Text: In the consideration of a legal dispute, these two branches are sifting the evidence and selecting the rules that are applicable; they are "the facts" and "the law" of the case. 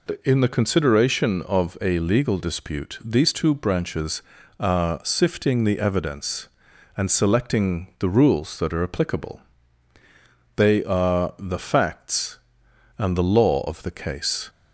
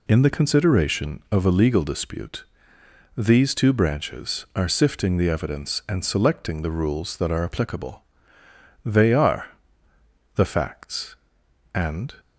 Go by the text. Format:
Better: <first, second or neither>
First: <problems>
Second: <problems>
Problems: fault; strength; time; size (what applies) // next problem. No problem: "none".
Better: first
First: none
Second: pauses between "are" and "the"; noticeable; at 9.4 s; 0.86 s long // stops before "the law of the case"; at 12.1 s